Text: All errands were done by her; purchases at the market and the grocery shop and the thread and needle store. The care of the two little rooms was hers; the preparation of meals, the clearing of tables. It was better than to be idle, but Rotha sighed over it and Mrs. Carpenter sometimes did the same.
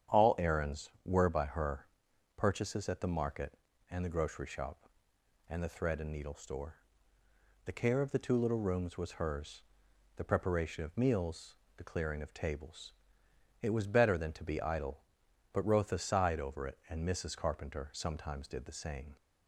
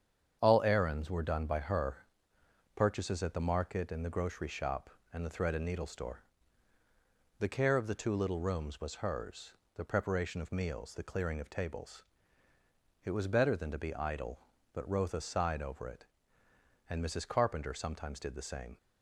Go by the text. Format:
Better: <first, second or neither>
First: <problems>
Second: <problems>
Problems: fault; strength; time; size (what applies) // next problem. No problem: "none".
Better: second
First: starts louder than the rest; strong; until 1.3 s; 9 dB // skips "done"; at 1.2 s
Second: starts louder than the rest; strong; until 1.4 s; 8 dB